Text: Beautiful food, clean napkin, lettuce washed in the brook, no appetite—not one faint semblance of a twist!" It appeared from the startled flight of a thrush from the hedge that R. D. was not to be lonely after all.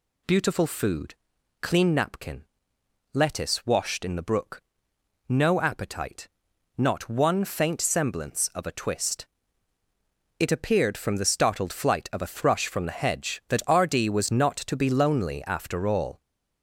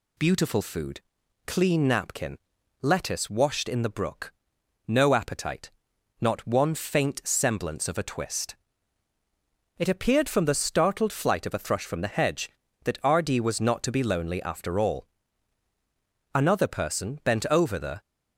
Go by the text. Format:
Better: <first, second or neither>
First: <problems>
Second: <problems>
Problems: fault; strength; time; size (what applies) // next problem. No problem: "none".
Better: first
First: none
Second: goes on to say "Another person bent over the"; strong; from 16.3 s on; 1.6 s long